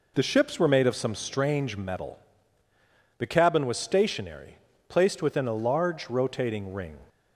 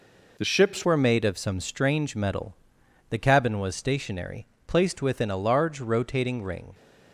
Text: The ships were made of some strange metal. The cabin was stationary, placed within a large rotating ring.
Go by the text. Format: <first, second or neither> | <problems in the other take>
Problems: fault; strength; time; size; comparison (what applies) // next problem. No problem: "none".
first | changes voice at "were"; from 0.8 s on; 5.9 s long